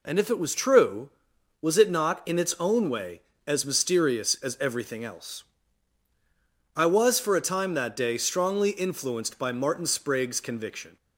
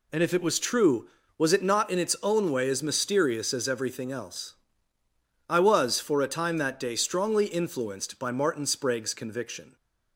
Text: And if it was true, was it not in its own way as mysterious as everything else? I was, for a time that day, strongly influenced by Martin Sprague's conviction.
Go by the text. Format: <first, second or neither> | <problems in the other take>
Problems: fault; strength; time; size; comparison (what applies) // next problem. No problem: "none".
neither | none